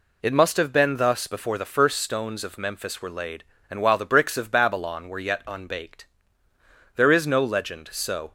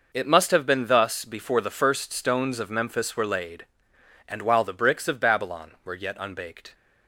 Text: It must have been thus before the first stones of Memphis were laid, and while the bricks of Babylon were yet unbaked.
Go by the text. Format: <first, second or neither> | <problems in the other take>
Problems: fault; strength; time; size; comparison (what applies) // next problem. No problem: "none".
second | goes on to say "There is no legend so"; from 6.9 s on; 1.3 s long